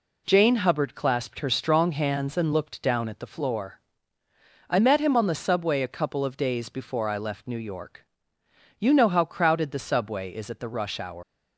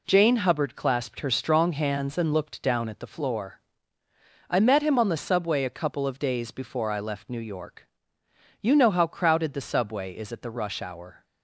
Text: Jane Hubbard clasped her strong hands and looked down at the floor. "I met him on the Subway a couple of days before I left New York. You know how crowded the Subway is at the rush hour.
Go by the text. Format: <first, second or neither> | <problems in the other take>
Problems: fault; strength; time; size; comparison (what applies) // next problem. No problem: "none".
second | leaves "hour" unfinished; at 11.2 s; 190 ms